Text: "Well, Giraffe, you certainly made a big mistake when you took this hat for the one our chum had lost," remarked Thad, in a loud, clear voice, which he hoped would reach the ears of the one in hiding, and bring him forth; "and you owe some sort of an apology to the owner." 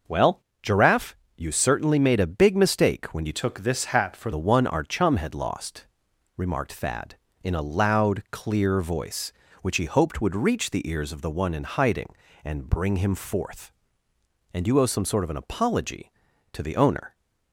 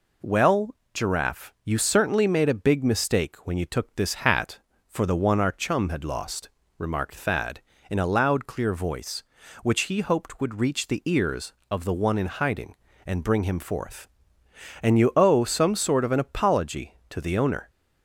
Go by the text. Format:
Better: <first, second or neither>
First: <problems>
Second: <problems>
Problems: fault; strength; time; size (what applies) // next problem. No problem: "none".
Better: second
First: changes voice from "took" to "for"; from 3.3 to 4.3 s; 1.0 s long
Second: none